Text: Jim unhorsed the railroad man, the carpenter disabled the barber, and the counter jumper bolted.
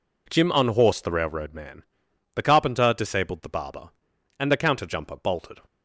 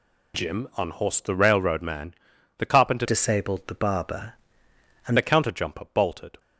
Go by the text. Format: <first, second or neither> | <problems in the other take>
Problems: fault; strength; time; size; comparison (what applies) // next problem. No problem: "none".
first | changes voice from "disabled" to "and"; from 3.0 to 5.1 s; 2.1 s long